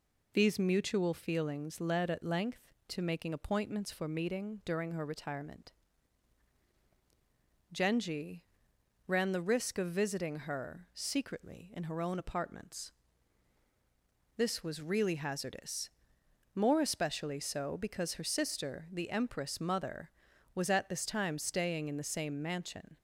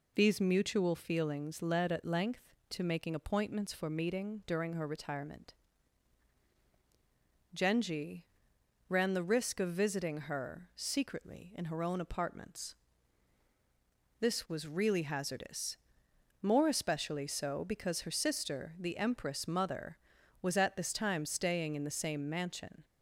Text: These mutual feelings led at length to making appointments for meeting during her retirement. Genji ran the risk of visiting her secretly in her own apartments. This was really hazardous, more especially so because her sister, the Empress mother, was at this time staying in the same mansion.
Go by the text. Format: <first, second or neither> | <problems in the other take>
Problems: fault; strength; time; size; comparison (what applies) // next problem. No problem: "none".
neither | pauses between "Genji" and "ran"; noticeable; the same in both